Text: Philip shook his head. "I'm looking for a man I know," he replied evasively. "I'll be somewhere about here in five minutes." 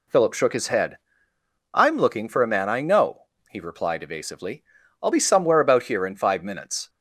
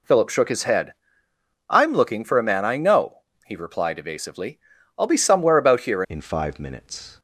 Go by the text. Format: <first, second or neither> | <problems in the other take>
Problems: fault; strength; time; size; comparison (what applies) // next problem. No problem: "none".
first | changes voice at "in"; from 6.0 s on; 1.1 s long